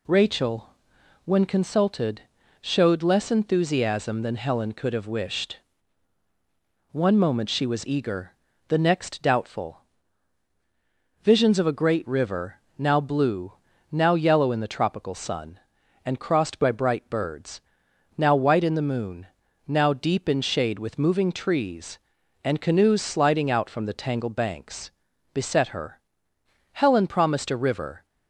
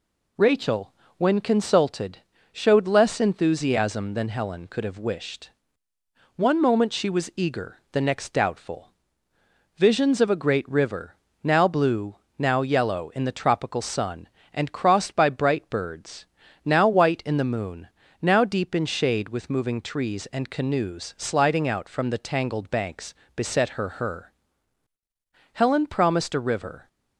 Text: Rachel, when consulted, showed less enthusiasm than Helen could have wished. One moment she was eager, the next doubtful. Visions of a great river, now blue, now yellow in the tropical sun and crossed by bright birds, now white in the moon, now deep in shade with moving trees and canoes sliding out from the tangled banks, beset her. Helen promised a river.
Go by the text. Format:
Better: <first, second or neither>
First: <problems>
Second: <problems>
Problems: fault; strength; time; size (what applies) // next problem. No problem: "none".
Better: first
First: none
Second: says "her" twice; at 23.8 s